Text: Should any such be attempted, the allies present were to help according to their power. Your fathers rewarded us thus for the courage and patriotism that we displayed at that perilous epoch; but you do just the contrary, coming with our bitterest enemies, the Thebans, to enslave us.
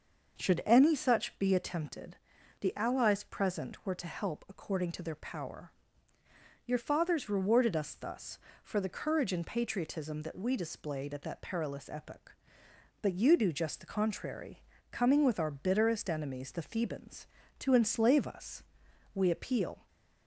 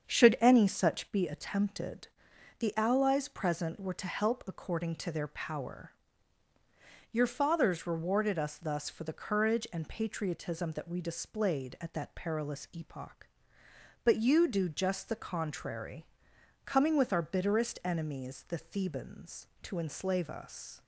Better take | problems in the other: second | starts louder than the rest; noticeable; until 1.4 s; 6 dB; strong in the second // goes on to say "We appeal"; noticeable; from 19.1 s on; 0.72 s long

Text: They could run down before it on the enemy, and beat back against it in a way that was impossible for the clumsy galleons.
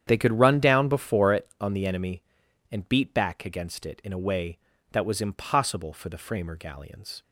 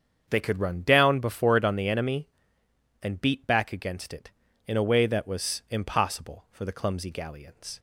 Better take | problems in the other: second | starts louder than the rest; strong; until 1.0 s; 9 dB; strong in the second // says "framer" for "clumsy"; at 6.1 s

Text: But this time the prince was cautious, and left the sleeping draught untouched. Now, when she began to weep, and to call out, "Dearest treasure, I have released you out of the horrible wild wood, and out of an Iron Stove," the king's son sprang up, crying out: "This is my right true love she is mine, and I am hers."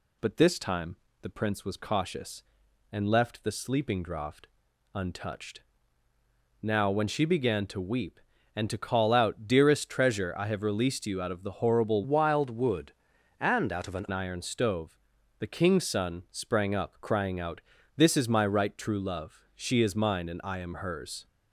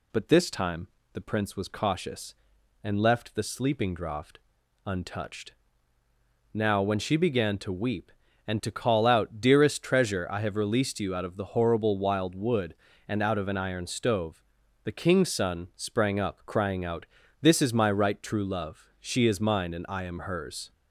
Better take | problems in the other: second | pauses between "time" and "the"; slight; at 0.9 s; 0.24 s long; slight in the second // pauses between "draught" and "untouched"; noticeable; at 4.4 s; 0.48 s long; noticeable in the second // changes voice from "wild" to "an"; from 12.0 to 14.0 s; 2.0 s long

